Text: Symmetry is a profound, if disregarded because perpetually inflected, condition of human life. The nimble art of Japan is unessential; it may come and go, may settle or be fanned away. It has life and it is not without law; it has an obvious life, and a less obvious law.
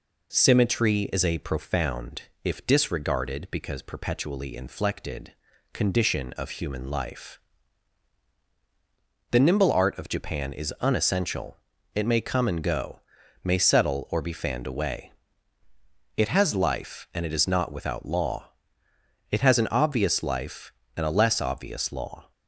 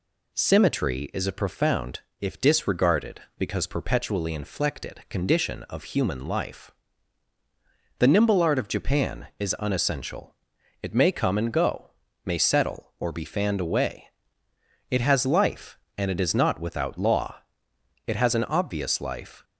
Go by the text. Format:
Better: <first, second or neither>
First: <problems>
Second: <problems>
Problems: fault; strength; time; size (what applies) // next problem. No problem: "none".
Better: first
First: none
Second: stops before "and a less obvious law"; at 19.4 s